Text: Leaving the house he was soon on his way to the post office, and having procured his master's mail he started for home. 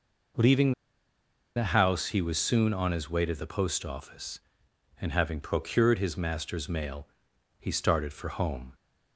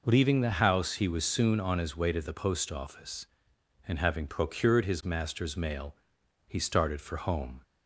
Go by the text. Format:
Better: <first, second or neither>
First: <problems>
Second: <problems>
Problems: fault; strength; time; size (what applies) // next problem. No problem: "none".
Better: second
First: pauses between "Leaving" and "the"; noticeable; at 0.7 s; 0.82 s long // pauses between "mail" and "he"; noticeable; at 7.0 s; 0.52 s long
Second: pauses between "mail" and "he"; noticeable; at 5.9 s; 0.52 s long